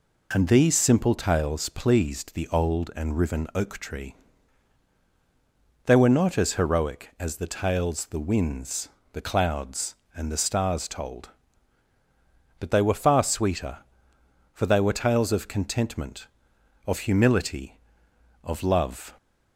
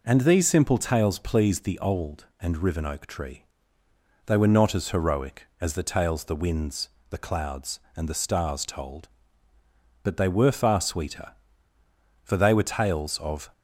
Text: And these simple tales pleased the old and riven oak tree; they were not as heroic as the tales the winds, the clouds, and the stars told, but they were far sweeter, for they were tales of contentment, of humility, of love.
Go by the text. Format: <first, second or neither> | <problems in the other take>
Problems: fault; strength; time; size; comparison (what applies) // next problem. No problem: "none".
first | stops before "contentment of humility of love"; at 13.5 s